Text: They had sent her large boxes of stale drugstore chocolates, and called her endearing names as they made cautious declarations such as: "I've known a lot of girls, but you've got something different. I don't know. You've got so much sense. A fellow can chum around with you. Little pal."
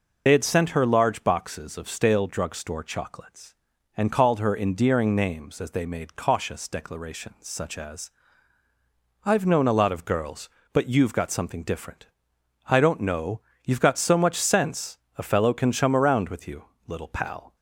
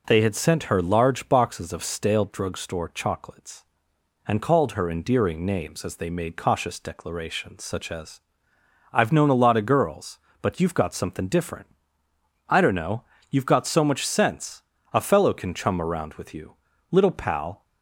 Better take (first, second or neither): second